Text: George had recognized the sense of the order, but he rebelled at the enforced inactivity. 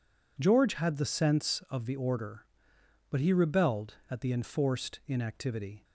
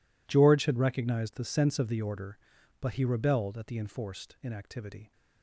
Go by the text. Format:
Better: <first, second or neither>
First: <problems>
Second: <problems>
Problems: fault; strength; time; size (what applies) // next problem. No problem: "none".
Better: second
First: skips "recognized"; at 0.9 s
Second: none